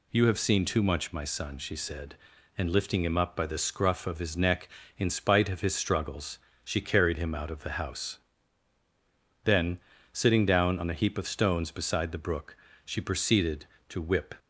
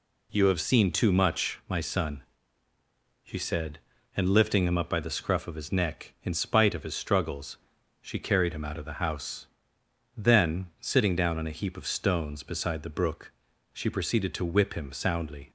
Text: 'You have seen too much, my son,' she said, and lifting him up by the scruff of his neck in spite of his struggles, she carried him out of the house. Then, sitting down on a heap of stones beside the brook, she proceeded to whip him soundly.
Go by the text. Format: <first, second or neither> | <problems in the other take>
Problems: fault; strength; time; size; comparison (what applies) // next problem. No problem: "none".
second | stops before "him soundly"; at 14.3 s